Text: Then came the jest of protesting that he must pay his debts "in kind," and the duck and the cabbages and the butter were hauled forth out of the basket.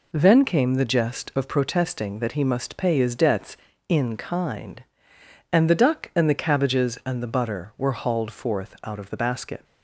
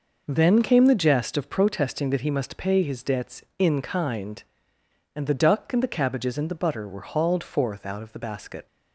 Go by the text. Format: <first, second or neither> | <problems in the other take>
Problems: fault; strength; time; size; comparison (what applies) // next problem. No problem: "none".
neither | none